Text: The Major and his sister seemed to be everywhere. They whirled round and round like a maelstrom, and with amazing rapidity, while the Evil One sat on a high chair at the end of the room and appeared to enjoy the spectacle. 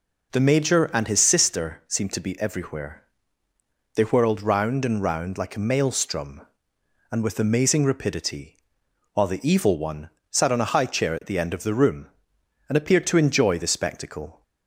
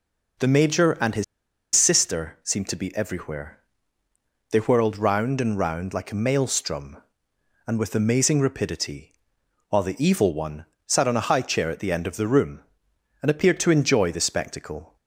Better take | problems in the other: first | pauses between "his" and "sister"; noticeable; at 1.2 s; 0.51 s long // pauses between "One" and "sat"; slight; at 10.6 s; 0.22 s long; slight in the first

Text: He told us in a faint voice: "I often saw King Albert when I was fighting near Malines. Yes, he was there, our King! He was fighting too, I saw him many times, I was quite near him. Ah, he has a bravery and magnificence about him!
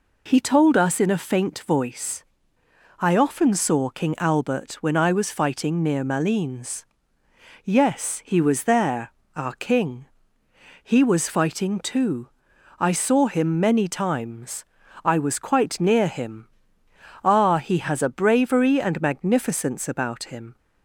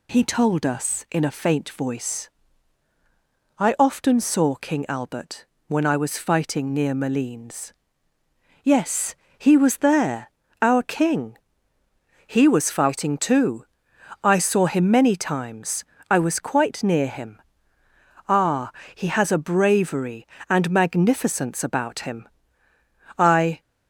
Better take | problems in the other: first | pauses between "Albert" and "when"; slight; at 5.4 s; 0.22 s long // goes on to say "I"; slight; from 23.1 s on; 0.44 s long

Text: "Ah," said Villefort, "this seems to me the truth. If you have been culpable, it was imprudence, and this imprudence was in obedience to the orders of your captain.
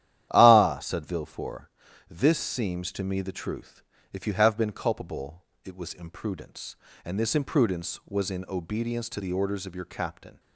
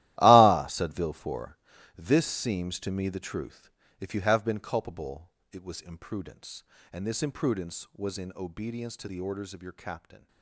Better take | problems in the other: first | gets quieter; strong; throughout; 13.5 dB // starts louder than the rest; strong; until 1.2 s; 15 dB; strong in the first

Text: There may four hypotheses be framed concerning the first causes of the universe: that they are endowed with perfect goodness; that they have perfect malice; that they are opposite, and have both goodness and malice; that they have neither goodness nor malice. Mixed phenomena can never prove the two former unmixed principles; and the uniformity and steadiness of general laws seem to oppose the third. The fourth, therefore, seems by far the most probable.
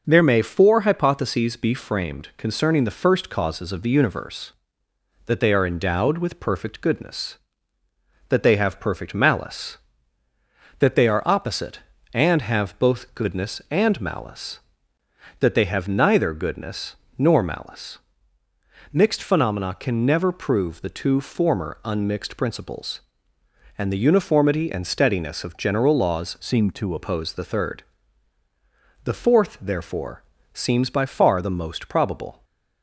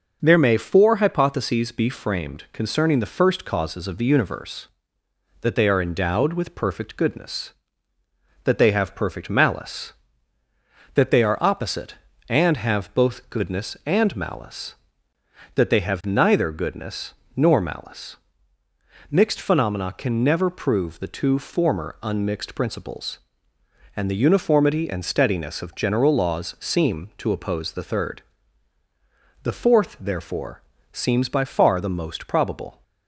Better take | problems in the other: second | starts louder than the rest; noticeable; until 1.0 s; 6 dB; noticeable in the second // pauses between "goodness" and "nor"; slight; at 16.9 s; 0.20 s long; slight in the second // changes voice from "seem" to "to"; from 26.4 to 26.9 s; 0.5 s long // stays silent after the last word; slight; from 32.3 s on; 0.5 s long

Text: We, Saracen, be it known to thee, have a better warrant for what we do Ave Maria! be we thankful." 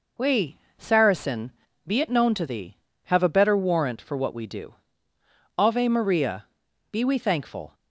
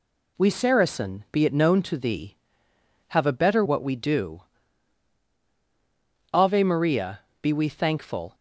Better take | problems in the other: first | skips "warrant for"; at 3.6 s // pauses between "do" and "Ave"; strong; at 4.4 s; 1.9 s long; noticeable in the first

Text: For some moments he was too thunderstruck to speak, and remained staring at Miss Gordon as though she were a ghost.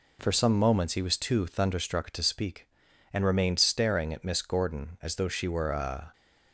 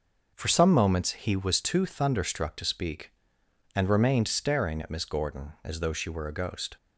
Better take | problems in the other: second | stops before "ghost"; at 6.1 s

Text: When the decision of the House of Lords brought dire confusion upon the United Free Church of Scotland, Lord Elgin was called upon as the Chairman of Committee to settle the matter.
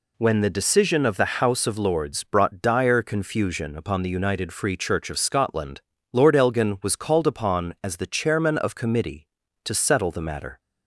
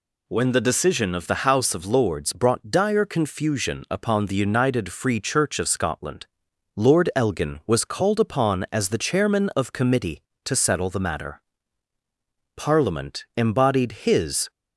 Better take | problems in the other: first | goes on to say "Parliament embodied his"; strong; from 12.5 s on; 1.9 s long

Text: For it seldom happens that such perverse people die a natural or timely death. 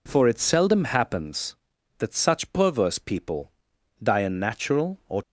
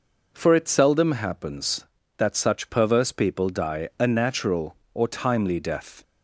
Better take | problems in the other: second | pauses between "people" and "die"; noticeable; at 3.5 s; 0.50 s long // stops before "timely death"; at 5.2 s

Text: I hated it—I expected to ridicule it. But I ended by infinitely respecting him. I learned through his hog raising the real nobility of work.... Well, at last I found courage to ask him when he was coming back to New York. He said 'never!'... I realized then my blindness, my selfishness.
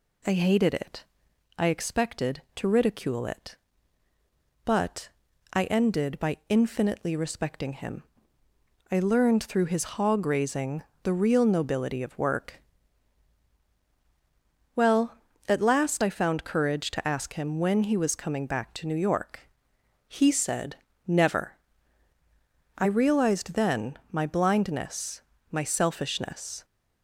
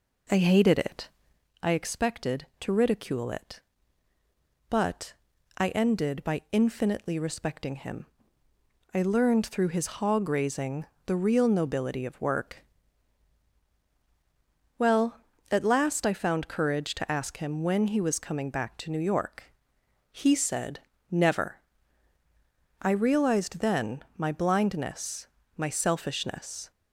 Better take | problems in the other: first | starts louder than the rest; until 1.4 s; 3.5 dB // pauses between "But" and "I"; noticeable; at 5.1 s; 0.46 s long; noticeable in the first // pauses between "raising" and "the"; slight; at 10.8 s; 0.22 s long; slight in the first // pauses between "said" and "never"; slight; at 20.8 s; 0.30 s long; slight in the first

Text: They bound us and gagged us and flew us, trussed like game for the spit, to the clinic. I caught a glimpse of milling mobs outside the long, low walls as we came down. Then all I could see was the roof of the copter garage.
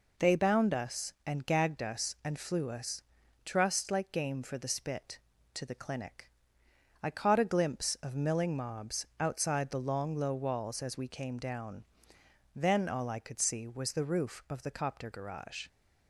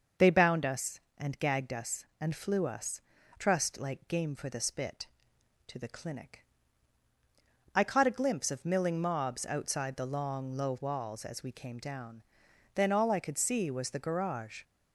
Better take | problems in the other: first | starts louder than the rest; until 1.3 s; 6 dB // skips "roof of the copter"; at 13.9 s

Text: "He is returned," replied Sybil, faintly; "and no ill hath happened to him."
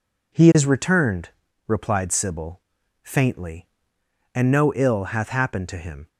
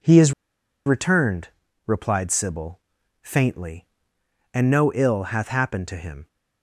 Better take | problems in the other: first | pauses between "is" and "returned"; noticeable; at 0.3 s; 0.53 s long

